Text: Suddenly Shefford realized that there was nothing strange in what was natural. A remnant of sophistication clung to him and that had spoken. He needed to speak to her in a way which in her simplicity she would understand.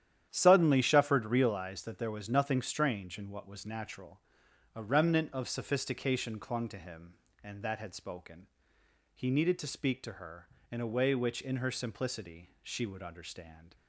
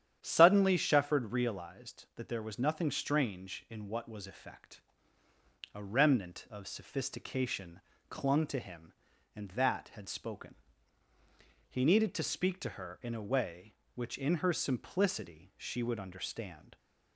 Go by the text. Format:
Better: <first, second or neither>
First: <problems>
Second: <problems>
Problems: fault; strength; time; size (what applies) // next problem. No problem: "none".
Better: first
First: starts louder than the rest; strong; until 1.3 s; 10.5 dB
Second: starts louder than the rest; strong; until 1.2 s; 10 dB // says "effect" for "natural"; at 4.2 s // pauses between "sophistication" and "clung"; slight; at 7.8 s; 0.26 s long